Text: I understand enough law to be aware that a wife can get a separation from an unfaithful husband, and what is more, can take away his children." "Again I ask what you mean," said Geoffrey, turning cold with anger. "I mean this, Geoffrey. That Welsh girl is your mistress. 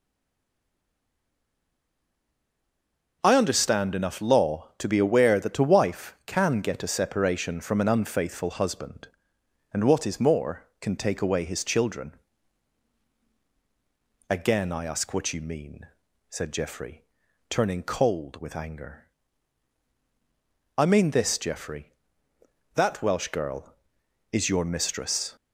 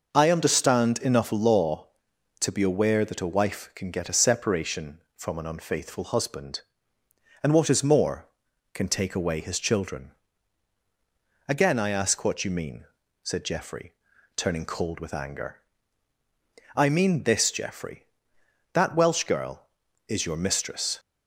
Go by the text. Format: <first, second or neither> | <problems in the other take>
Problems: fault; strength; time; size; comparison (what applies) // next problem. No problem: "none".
second | stays silent before the first word; strong; until 3.2 s; 3.2 s long